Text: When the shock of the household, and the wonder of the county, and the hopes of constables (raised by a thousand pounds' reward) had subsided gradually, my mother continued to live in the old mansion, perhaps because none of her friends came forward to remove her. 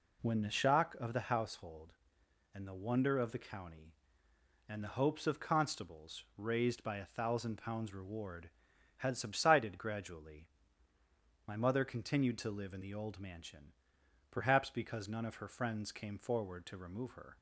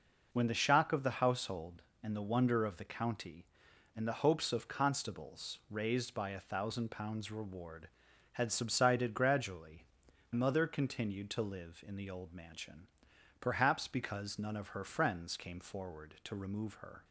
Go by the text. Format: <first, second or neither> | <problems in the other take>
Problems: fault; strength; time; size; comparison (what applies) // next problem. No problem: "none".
first | skips "my"; at 10.0 s